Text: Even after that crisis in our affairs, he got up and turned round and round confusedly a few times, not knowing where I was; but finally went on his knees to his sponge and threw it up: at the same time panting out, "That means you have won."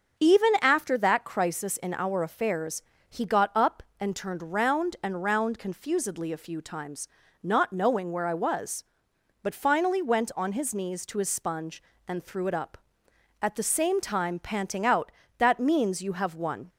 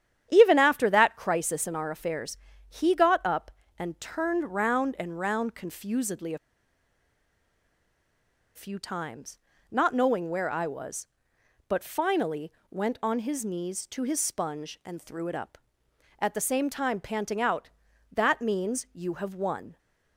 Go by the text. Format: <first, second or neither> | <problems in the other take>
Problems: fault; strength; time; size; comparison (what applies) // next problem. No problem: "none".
first | starts louder than the rest; strong; until 1.3 s; 9.5 dB; also in the first // pauses between "a" and "few"; strong; at 6.3 s; 2.1 s long // pauses between "finally" and "went"; slight; at 12.5 s; 0.18 s long